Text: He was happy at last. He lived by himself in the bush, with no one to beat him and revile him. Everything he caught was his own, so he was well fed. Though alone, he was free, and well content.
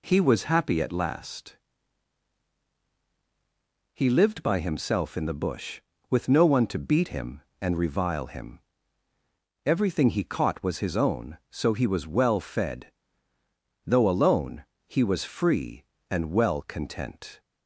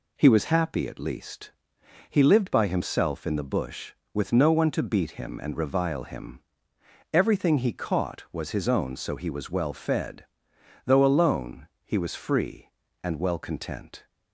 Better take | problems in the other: first | says "least" for "last"; at 0.9 s

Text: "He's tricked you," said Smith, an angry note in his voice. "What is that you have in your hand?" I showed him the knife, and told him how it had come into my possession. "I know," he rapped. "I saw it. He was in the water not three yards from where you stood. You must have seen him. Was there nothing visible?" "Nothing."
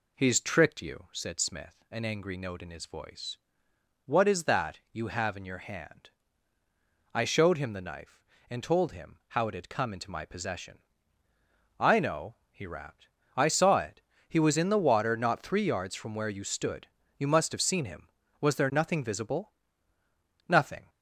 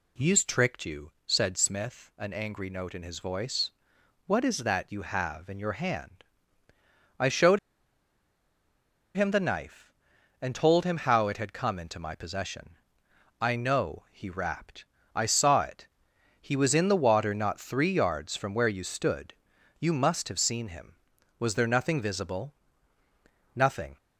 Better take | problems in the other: first | pauses between "showed" and "him"; strong; at 7.5 s; 1.5 s long

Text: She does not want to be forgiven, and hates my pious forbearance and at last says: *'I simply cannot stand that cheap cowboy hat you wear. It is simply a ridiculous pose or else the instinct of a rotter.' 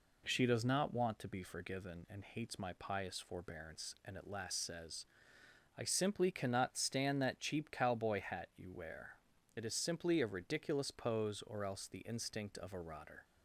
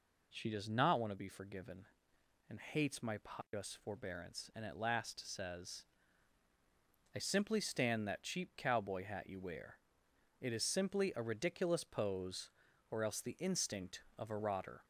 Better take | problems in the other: first | skips "cannot"; at 7.5 s

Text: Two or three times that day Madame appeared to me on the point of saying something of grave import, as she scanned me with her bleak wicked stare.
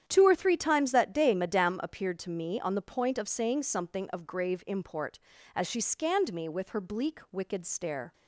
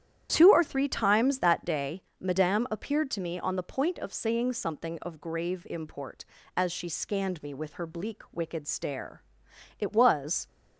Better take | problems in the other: first | starts louder than the rest; strong; until 1.3 s; 10 dB; strong in the first // pauses between "day" and "Madame"; slight; at 2.0 s; 0.18 s long // goes on to say "It was"; noticeable; from 9.8 s on; 0.66 s long

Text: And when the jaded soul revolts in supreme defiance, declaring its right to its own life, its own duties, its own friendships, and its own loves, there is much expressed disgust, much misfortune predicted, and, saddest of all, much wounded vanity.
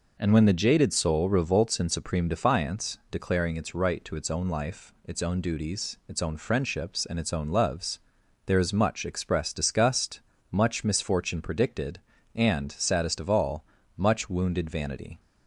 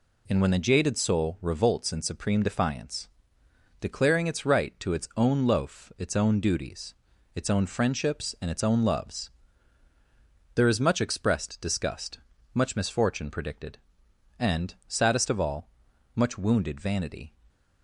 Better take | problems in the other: first | says "loaf" for "life"; at 5.4 s

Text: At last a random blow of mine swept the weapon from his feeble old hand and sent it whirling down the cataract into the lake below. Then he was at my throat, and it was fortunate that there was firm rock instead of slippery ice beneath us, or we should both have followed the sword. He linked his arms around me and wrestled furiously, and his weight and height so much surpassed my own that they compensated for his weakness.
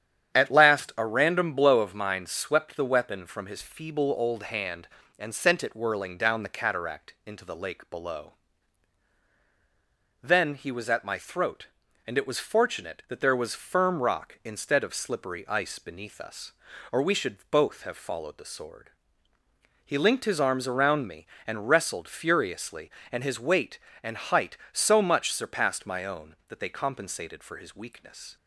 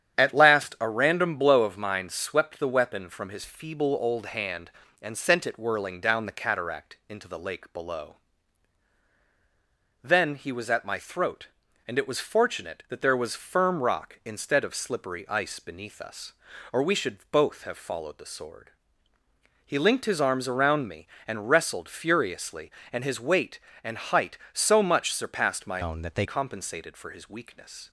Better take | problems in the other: first | starts louder than the rest; strong; until 1.2 s; 9.5 dB; strong in the first // changes voice from "own" to "they"; from 25.8 to 26.2 s; 0.4 s long

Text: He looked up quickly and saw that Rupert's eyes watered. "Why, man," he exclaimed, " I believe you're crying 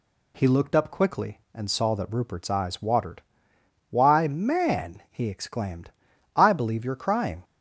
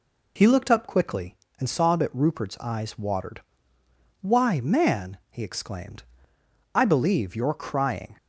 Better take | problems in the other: neither | none

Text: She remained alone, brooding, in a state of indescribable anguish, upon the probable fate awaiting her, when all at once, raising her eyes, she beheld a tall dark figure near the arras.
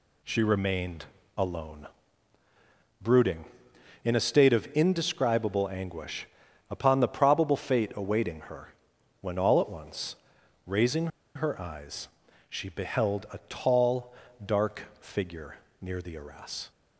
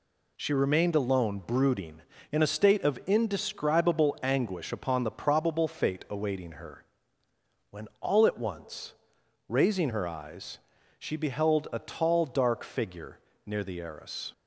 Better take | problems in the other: second | pauses between "remained" and "alone"; slight; at 1.0 s; 0.30 s long // pauses between "raising" and "her"; slight; at 11.0 s; 0.27 s long // pauses between "tall" and "dark"; slight; at 14.1 s; 0.32 s long // pauses between "dark" and "figure"; slight; at 14.8 s; 0.16 s long // pauses between "figure" and "near"; slight; at 15.5 s; 0.24 s long; slight in the second

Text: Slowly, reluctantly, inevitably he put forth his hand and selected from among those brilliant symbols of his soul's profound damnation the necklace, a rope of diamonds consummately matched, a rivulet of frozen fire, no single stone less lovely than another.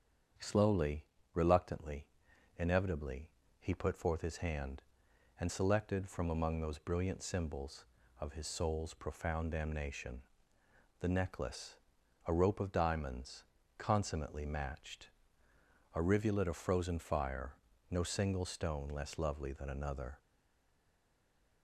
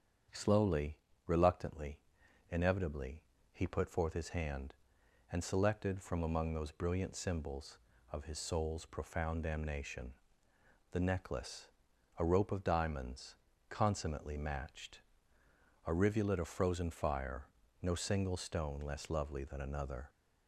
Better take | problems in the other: second | starts louder than the rest; strong; until 1.6 s; 8 dB; strong in the second // pauses between "inevitably" and "he"; slight; at 3.3 s; 0.28 s long; slight in the second // pauses between "damnation" and "the"; noticeable; at 10.2 s; 0.78 s long; noticeable in the second // pauses between "diamonds" and "consummately"; slight; at 13.4 s; 0.32 s long; slight in the second // stays silent after the last word; noticeable; from 20.1 s on; 1.5 s long

